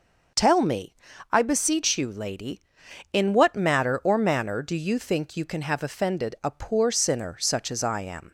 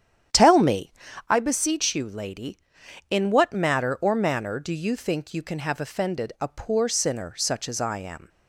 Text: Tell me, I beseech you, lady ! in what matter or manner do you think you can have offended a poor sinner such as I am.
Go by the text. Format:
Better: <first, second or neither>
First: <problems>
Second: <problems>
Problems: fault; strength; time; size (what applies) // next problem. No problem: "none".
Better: first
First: none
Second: starts louder than the rest; strong; until 1.3 s; 9.5 dB